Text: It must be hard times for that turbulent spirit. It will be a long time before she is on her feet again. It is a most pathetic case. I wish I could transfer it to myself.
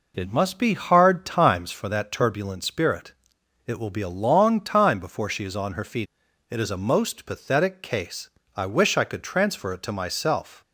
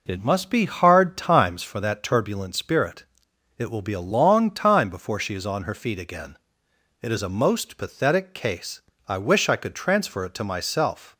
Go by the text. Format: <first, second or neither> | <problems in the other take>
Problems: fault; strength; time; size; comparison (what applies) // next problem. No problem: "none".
second | skips "again"; at 6.2 s